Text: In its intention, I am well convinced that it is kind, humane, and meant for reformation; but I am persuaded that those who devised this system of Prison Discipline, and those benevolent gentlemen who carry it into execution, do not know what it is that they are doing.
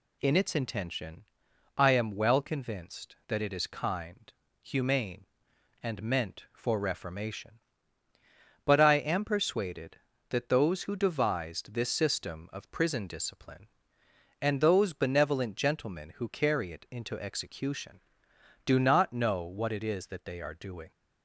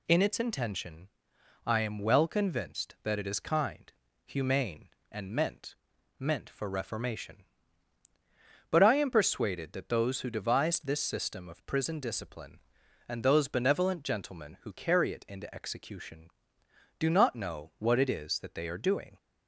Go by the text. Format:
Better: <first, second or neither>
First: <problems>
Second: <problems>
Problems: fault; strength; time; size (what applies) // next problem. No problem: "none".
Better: first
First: none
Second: says "meant" twice; at 6.1 s